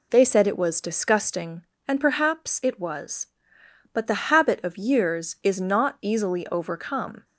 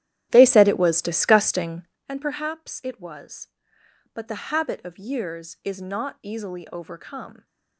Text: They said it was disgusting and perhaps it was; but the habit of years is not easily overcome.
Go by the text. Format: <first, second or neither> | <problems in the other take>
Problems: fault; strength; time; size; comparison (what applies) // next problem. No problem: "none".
first | starts louder than the rest; strong; until 2.1 s; 12.5 dB